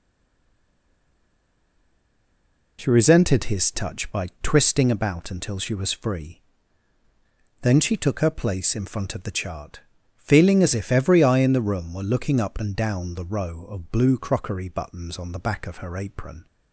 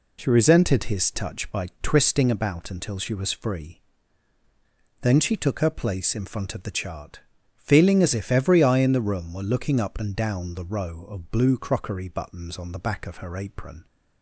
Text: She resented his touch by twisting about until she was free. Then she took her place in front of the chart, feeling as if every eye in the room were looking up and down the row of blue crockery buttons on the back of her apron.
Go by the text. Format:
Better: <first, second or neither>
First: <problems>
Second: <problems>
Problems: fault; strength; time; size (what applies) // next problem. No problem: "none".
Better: second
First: stays silent before the first word; strong; until 2.7 s; 2.7 s long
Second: none